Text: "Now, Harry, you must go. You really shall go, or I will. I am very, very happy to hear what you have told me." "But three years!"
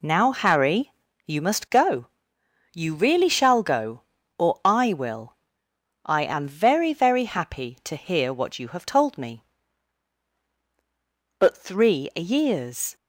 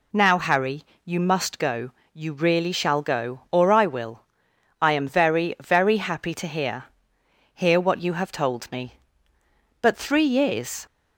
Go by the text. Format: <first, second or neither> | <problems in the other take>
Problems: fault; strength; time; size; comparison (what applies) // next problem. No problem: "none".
first | says "hear" twice; at 7.5 s